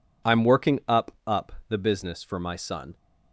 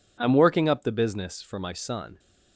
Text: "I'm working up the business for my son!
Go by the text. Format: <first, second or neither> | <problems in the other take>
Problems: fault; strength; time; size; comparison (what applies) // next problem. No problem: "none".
second | says "up" twice; at 1.2 s